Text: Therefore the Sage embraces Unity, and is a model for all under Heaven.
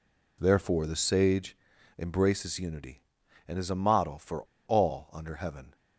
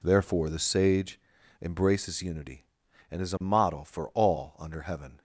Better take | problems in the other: second | pauses between "Sage" and "embraces"; at 1.5 s; 0.40 s long; also in the second // pauses between "for" and "all"; slight; at 4.4 s; 0.22 s long

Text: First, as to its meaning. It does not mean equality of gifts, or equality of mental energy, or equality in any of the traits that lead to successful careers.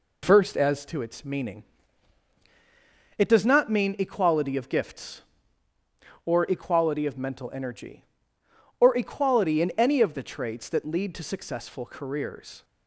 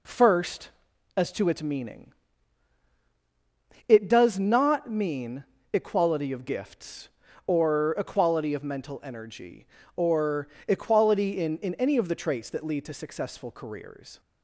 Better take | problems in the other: first | pauses between "mean" and "equality"; slight; at 5.4 s; 0.30 s long // pauses between "or" and "equality"; slight; at 10.4 s; 0.22 s long // says "in" twice; at 11.5 s

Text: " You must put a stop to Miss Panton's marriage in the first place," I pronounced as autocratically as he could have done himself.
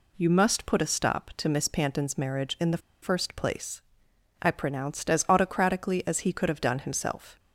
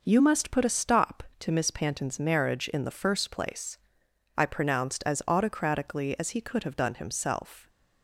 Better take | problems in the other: second | pauses between "the" and "first"; slight; at 2.7 s; 0.22 s long

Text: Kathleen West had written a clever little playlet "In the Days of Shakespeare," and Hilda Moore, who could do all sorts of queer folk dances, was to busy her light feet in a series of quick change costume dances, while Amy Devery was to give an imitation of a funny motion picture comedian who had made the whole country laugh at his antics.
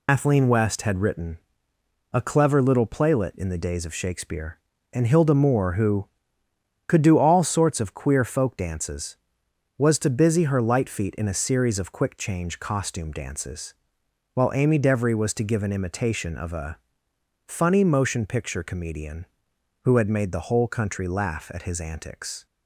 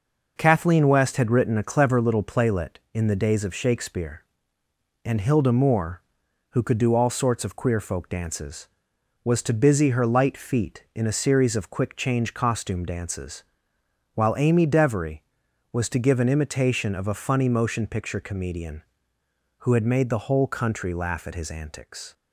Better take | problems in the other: second | loses the start of "Kathleen"; at 0.0 s; 130 ms // pauses between "written" and "a"; noticeable; at 1.3 s; 0.74 s long // pauses between "a" and "funny"; noticeable; at 16.7 s; 0.68 s long

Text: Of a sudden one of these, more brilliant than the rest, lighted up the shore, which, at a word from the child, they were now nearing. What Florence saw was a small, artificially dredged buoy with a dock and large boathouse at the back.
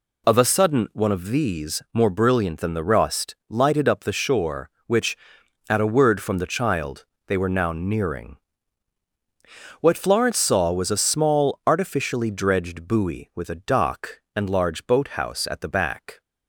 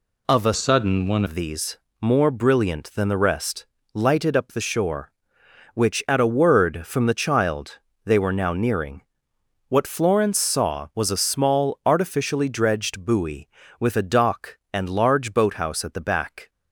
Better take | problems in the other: first | changes voice from "sudden" to "one"; from 0.5 to 1.2 s; 0.7 s long

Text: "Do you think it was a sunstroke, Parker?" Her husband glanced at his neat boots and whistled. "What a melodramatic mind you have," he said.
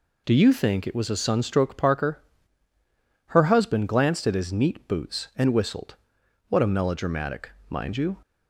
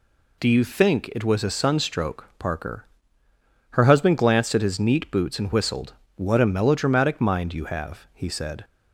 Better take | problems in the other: second | pauses between "melodramatic" and "mind"; slight; at 7.5 s; 0.18 s long // stops before "have he said"; at 8.2 s

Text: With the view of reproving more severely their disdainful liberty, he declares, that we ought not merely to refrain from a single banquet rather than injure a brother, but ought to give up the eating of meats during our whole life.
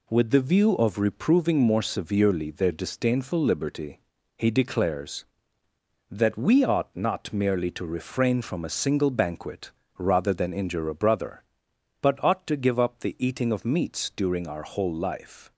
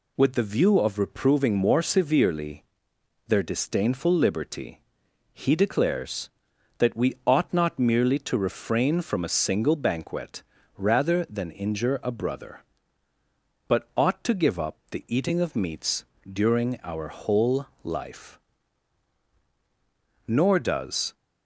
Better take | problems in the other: first | pauses between "severely" and "their"; noticeable; at 2.6 s; 0.64 s long // pauses between "banquet" and "rather"; slight; at 10.4 s; 0.34 s long; slight in the first // pauses between "meats" and "during"; slight; at 16.0 s; 0.28 s long // pauses between "whole" and "life"; slight; at 17.6 s; 0.16 s long // goes on to say "Nor does"; noticeable; from 20.2 s on; 0.86 s long

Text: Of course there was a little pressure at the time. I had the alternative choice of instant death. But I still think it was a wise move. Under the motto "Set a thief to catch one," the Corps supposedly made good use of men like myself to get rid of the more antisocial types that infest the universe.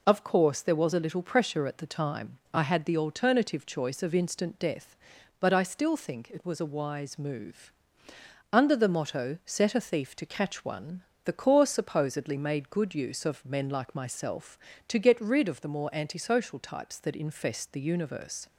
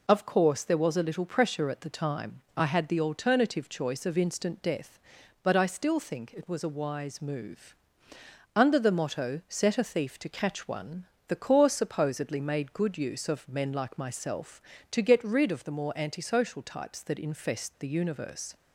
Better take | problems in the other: neither | none

